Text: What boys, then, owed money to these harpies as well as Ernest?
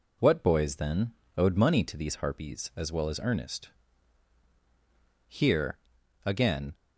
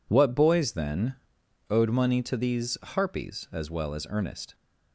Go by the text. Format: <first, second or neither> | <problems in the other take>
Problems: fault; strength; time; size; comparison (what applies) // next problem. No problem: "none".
second | goes on to say "Here again"; from 5.2 s on; 1.4 s long